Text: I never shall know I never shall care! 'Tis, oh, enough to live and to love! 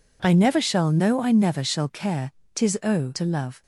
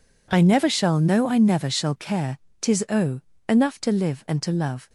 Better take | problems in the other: second | skips "enough to live and"; at 3.1 s

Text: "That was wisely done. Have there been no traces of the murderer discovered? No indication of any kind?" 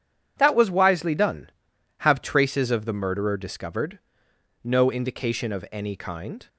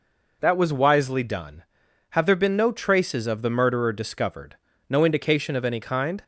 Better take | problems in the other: second | skips "there been no"; at 2.1 s

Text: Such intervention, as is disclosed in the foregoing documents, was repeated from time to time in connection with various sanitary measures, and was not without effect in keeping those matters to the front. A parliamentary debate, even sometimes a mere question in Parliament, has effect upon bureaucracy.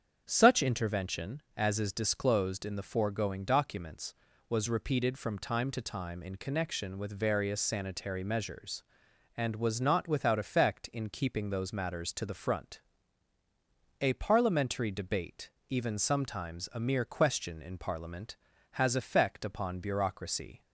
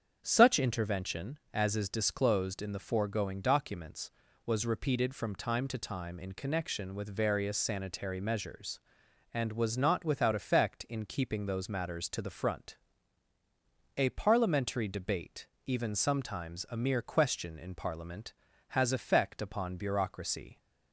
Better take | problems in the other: neither | starts louder than the rest; strong; the same in both

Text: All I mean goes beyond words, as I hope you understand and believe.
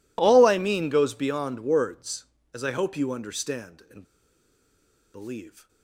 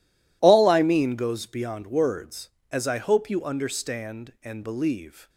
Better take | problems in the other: second | pauses between "and" and "believe"; at 4.0 s; 1.1 s long

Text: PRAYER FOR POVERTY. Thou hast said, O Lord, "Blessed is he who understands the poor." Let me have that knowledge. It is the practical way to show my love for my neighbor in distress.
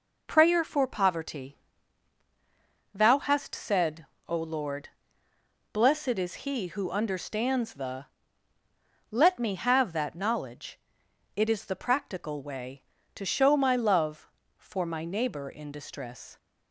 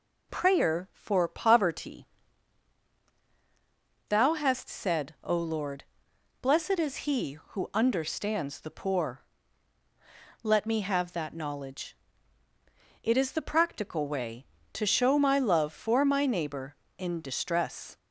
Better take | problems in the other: second | skips "poor"; at 8.5 s

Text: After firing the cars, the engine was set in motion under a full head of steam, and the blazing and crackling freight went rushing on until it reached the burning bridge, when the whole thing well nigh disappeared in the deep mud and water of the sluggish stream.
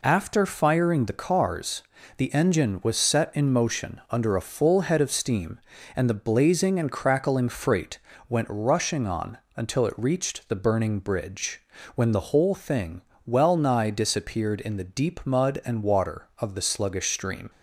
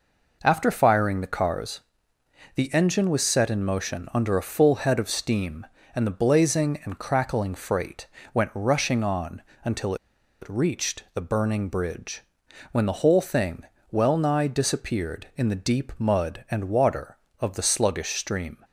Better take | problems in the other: first | pauses between "freight" and "went"; slight; at 8.0 s; 0.28 s long; slight in the first // pauses between "on" and "until"; slight; at 9.4 s; 0.22 s long; slight in the first // pauses between "until" and "it"; at 9.9 s; 0.45 s long // pauses between "thing" and "well"; slight; at 13.6 s; 0.28 s long; slight in the first

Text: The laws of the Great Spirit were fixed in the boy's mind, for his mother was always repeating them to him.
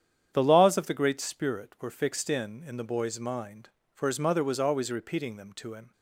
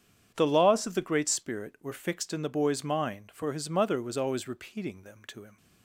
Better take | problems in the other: second | starts louder than the rest; strong; until 1.3 s; 8.5 dB; strong in the second // says "in" twice; at 2.6 s

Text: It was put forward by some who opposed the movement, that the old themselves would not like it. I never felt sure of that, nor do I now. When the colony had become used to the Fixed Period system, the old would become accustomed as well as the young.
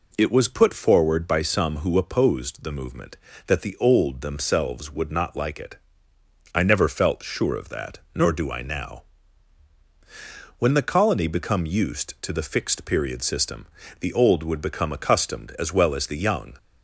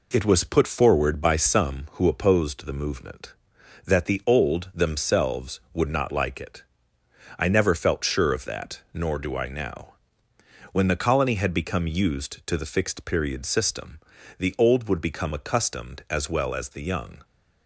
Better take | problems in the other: second | skips "had"; at 11.2 s

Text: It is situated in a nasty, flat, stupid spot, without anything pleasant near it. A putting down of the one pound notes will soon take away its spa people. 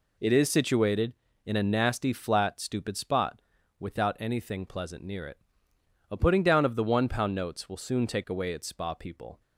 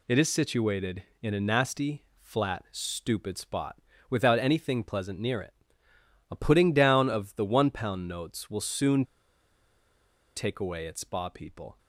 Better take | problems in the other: first | pauses between "soon" and "take"; strong; at 9.0 s; 1.3 s long

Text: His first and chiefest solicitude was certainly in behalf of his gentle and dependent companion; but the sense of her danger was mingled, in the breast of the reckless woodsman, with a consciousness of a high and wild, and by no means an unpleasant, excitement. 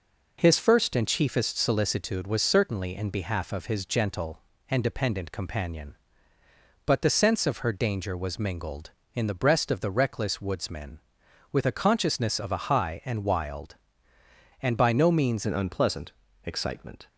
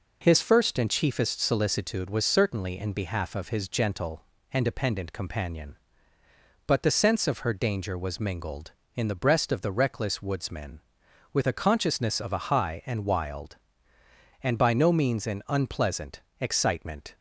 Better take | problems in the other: second | changes voice at "an"; from 15.4 s on; 1.6 s long

